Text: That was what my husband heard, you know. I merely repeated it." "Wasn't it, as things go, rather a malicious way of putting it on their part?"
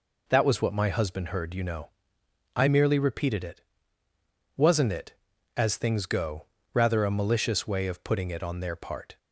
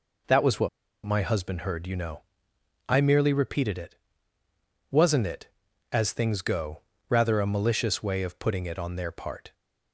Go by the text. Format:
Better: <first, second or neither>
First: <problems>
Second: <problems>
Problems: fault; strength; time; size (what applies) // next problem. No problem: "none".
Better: first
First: none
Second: pauses between "what" and "my"; slight; at 0.6 s; 0.36 s long